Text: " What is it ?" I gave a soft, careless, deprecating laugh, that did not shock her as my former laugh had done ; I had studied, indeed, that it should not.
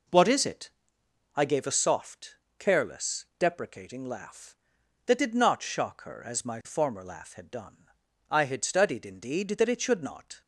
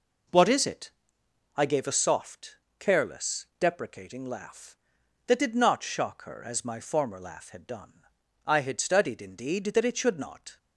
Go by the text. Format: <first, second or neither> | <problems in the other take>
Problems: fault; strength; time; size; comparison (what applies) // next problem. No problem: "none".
neither | none